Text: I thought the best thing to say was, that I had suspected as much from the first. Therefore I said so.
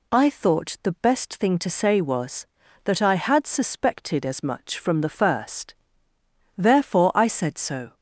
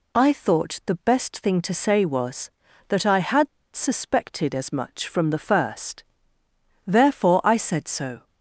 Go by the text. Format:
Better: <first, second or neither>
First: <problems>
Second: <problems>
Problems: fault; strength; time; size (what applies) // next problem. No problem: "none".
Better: first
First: none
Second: pauses between "had" and "suspected"; slight; at 3.4 s; 0.25 s long